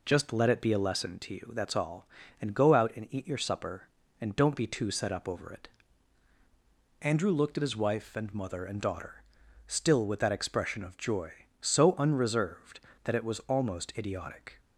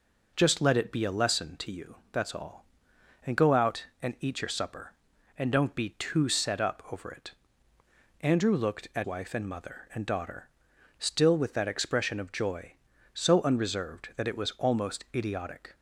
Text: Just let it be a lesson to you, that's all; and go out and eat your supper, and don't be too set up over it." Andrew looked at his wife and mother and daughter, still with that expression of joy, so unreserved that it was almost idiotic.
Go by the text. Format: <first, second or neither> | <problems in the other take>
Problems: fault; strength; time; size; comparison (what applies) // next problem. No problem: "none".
first | skips "his"; at 9.0 s